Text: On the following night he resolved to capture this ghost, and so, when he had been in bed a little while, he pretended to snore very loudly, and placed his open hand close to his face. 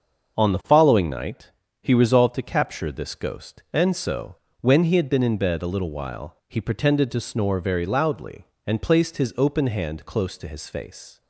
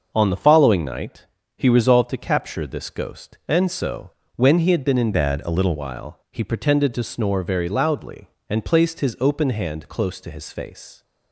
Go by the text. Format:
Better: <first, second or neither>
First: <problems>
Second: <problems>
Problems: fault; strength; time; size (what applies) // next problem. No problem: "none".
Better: first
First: starts louder than the rest; until 1.4 s; 6.5 dB // pauses between "night" and "he"; slight; at 1.4 s; 0.32 s long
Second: starts louder than the rest; until 1.1 s; 6.5 dB // pauses between "night" and "he"; slight; at 1.2 s; 0.32 s long // changes voice from "bed" to "little"; from 5.1 to 5.7 s; 0.6 s long